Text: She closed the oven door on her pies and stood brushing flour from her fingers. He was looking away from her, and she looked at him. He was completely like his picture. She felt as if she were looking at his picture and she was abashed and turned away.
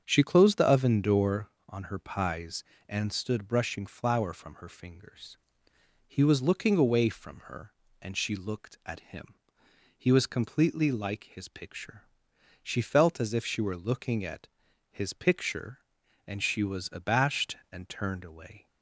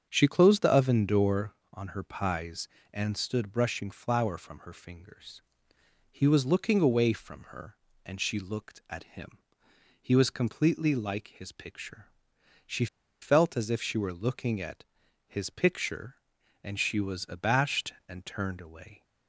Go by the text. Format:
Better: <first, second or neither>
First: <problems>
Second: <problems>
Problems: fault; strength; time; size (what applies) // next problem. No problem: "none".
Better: first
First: starts louder than the rest; strong; until 1.0 s; 7 dB // pauses between "at" and "his"; at 14.4 s; 0.44 s long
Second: starts louder than the rest; strong; until 1.1 s; 7 dB // pauses between "She" and "felt"; slight; at 12.8 s; 0.35 s long // pauses between "at" and "his"; at 14.8 s; 0.44 s long